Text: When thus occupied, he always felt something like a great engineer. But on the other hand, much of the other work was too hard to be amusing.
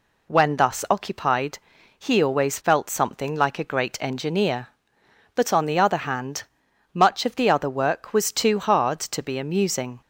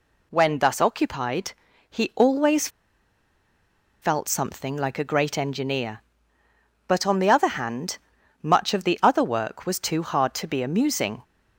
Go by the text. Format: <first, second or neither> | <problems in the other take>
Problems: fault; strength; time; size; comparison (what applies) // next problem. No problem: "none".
first | pauses between "always" and "felt"; strong; at 2.6 s; 1.3 s long